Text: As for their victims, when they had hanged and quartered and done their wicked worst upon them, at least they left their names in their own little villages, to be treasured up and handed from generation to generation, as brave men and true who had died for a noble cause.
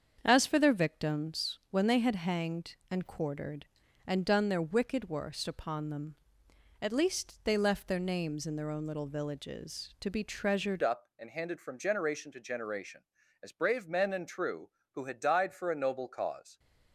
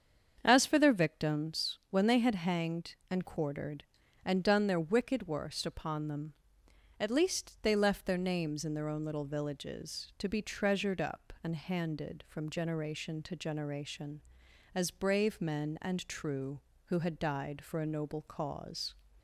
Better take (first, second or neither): second